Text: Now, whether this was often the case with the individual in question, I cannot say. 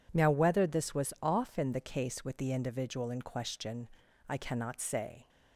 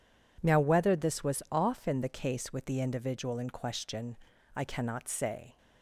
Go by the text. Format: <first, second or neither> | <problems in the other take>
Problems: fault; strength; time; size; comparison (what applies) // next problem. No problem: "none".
neither | none